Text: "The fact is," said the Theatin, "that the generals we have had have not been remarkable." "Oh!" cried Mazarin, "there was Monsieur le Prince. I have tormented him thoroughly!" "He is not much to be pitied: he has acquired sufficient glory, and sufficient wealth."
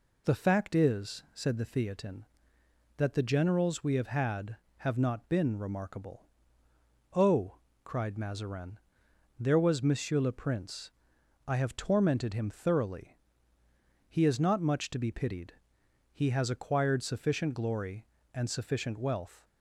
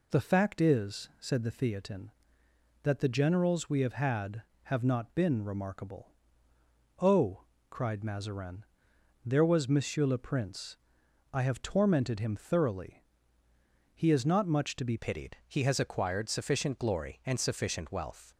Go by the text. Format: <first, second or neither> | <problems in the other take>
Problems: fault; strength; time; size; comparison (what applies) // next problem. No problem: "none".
first | changes voice at "pitied"; from 14.9 s on; 3.3 s long